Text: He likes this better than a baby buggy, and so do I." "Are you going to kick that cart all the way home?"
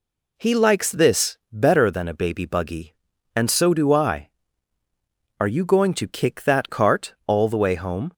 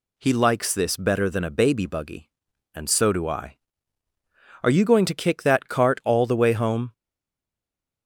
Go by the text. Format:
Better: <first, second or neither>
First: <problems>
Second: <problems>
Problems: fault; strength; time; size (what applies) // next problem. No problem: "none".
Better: first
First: none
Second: stays silent after the last word; from 6.9 s on; 1.1 s long